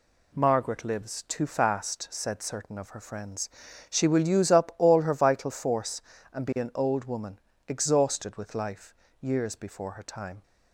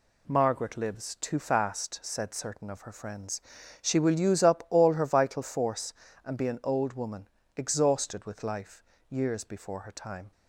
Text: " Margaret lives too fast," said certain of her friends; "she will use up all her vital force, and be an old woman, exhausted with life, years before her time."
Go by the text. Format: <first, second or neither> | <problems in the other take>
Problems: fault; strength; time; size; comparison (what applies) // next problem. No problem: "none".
neither | none